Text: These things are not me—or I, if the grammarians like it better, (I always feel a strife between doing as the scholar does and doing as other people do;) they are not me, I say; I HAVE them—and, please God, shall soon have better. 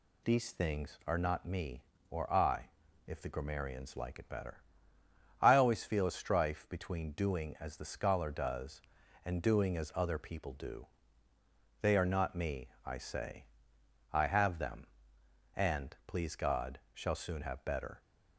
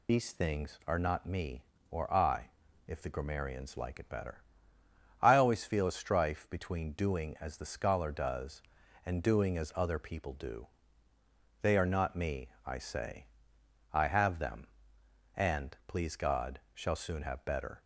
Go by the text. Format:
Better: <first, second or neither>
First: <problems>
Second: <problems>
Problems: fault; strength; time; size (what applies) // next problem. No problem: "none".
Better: first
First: none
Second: loses the start of "These"; at 0.0 s; 40 ms